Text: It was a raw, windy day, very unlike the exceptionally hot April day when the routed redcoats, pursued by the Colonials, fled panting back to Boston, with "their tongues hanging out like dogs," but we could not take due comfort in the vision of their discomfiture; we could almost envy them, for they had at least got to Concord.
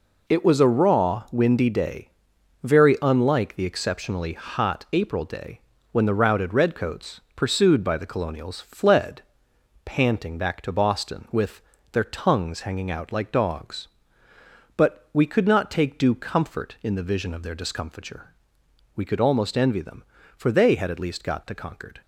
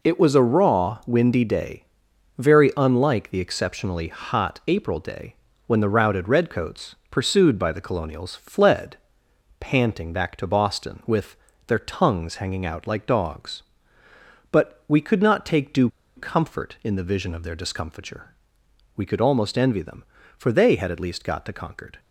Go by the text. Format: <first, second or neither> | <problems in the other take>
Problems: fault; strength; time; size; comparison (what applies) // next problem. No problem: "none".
first | pauses between "day" and "when"; slight; at 5.3 s; 0.32 s long; slight in the first // pauses between "fled" and "panting"; noticeable; at 8.9 s; 0.62 s long; noticeable in the first // pauses between "with" and "their"; slight; at 11.3 s; 0.32 s long; slight in the first // pauses between "due" and "comfort"; slight; at 15.8 s; 0.26 s long